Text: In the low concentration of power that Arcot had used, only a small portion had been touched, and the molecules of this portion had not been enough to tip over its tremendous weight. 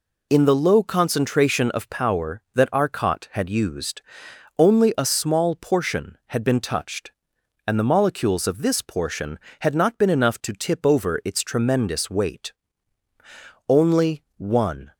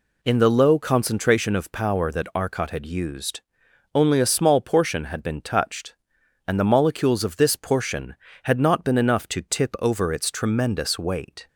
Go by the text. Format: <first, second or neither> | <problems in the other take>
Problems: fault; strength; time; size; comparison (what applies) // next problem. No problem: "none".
second | goes on to say "Only one"; noticeable; from 13.6 s on; 1.2 s long